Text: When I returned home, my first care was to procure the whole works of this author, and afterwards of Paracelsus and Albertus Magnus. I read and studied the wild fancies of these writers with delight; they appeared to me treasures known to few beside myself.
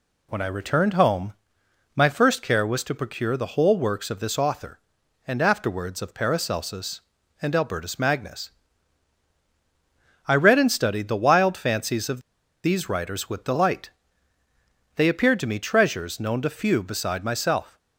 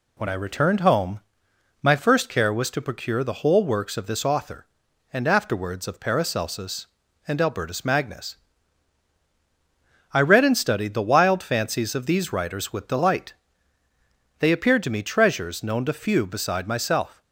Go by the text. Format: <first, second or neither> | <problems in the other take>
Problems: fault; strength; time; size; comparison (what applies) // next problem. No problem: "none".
second | pauses between "of" and "these"; at 12.1 s; 0.44 s long